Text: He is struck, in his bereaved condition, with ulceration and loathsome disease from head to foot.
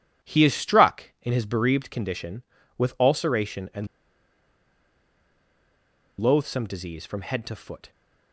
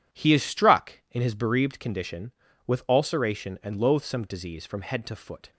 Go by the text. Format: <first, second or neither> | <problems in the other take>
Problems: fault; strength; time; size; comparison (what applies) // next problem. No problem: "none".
second | pauses between "and" and "loathsome"; strong; at 3.8 s; 2.3 s long